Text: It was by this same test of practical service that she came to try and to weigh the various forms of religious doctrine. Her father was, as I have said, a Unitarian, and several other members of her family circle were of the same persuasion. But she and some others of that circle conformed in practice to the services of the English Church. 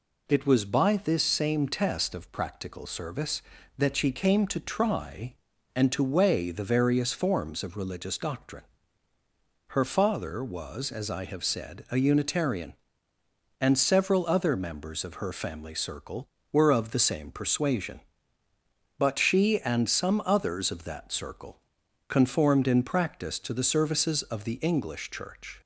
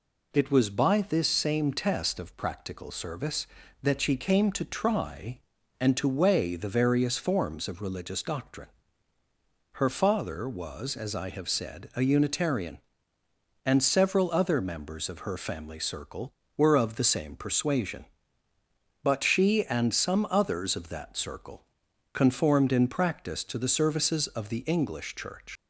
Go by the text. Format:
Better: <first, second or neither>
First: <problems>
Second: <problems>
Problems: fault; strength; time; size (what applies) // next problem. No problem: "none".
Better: first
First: pauses between "circle" and "conformed"; noticeable; at 21.5 s; 0.50 s long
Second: pauses between "circle" and "conformed"; noticeable; at 21.6 s; 0.50 s long // leaves "Church" unfinished; at 25.5 s; 100 ms